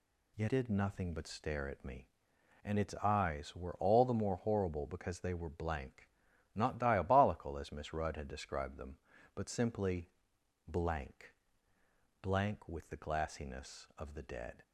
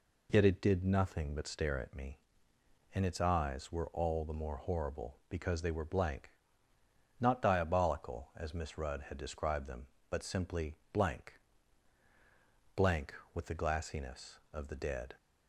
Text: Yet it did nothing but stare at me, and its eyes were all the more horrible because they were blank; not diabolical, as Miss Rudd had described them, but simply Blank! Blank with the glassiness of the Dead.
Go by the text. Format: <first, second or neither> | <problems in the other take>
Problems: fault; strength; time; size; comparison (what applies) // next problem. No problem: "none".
second | skips "it"; at 0.4 s // pauses between "simply" and "Blank"; noticeable; at 10.0 s; 0.58 s long; slight in the second